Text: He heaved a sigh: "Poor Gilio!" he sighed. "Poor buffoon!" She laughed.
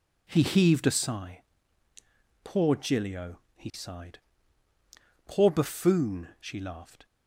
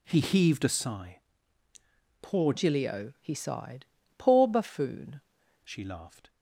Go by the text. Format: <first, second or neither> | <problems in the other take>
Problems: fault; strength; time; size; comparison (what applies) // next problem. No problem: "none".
first | changes voice from "Gilio" to "buffoon"; from 2.5 to 5.2 s; 2.7 s long